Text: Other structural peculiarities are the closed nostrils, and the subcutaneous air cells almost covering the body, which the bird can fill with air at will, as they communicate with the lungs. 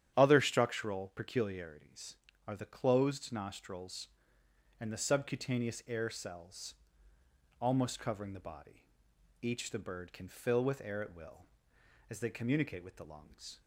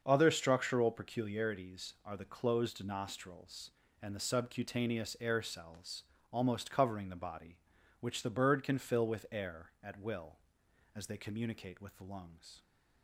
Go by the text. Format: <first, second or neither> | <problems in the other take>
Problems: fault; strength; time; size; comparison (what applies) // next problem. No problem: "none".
second | starts louder than the rest; strong; until 1.1 s; 10 dB; also in the second // pauses between "cells" and "almost"; noticeable; at 6.7 s; 0.88 s long; slight in the second // says "each" for "which"; at 9.4 s